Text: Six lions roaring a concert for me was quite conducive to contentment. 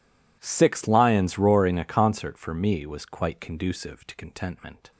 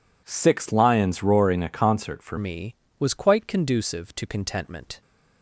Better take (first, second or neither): first